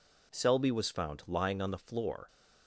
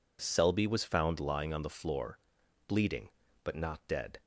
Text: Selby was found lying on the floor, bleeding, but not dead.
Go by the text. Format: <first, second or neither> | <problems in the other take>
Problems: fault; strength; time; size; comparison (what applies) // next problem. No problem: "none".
second | stops before "bleeding but not dead"; at 2.2 s